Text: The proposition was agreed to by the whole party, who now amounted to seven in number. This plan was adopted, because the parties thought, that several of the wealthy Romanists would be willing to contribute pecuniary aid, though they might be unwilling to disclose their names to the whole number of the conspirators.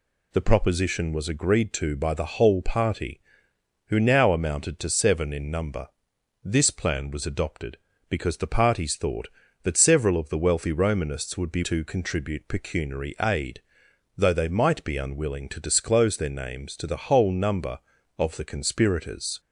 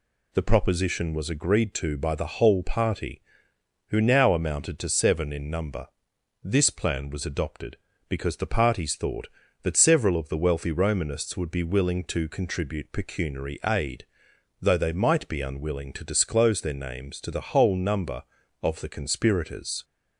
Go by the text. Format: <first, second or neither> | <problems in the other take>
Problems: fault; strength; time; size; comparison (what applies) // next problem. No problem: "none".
second | skips "willing"; at 11.6 s